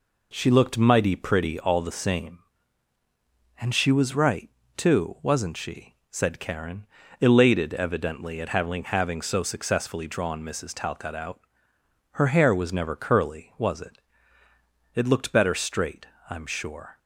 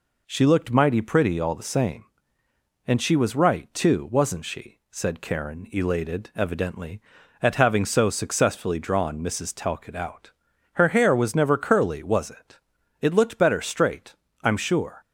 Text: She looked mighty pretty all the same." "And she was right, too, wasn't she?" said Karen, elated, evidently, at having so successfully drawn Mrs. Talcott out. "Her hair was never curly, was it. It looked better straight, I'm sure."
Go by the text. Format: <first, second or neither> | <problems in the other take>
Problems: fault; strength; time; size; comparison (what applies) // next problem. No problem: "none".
second | says "having" twice; at 8.8 s